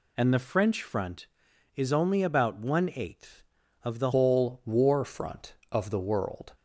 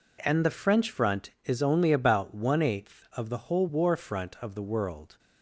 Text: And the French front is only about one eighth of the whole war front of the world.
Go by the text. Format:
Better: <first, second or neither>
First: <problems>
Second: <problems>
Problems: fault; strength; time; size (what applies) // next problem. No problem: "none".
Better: second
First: changes voice at "whole"; from 4.1 s on; 2.4 s long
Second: none